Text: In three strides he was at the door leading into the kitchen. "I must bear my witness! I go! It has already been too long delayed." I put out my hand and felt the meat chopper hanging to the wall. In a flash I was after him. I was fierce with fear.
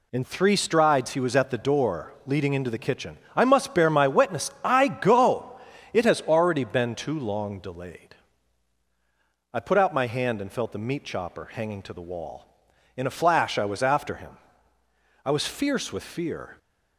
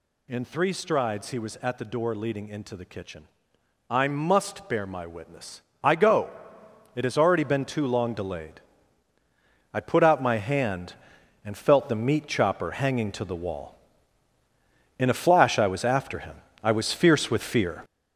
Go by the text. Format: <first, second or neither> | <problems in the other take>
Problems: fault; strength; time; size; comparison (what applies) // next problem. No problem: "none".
first | gets louder; strong; throughout; 7.5 dB